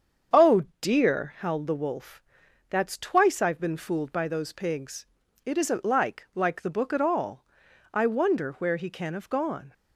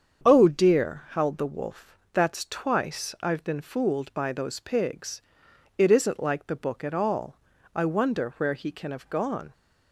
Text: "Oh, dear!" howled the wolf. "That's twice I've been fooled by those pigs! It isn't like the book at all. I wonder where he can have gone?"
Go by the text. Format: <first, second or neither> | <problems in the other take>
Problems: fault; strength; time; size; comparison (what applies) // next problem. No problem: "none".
second | starts louder than the rest; strong; until 1.5 s; 7.5 dB; strong in the second // says "like" twice; at 6.3 s